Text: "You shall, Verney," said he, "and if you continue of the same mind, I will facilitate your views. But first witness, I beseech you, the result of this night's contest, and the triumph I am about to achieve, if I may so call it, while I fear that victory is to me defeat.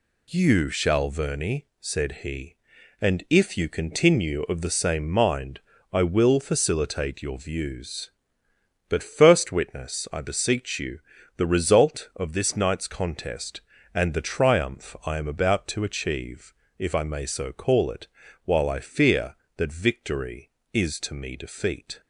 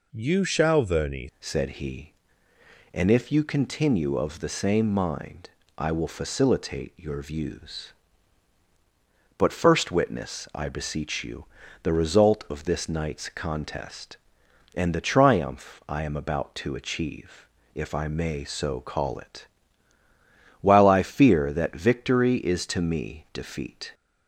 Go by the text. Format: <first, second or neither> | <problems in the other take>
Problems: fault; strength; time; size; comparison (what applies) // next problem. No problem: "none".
first | changes voice at "said"; from 1.4 s on; 22.5 s long